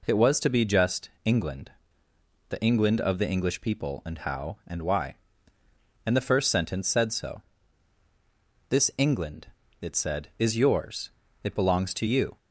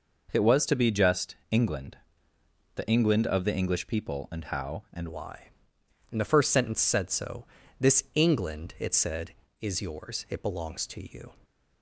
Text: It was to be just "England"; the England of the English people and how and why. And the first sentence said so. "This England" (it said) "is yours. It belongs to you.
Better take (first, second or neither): first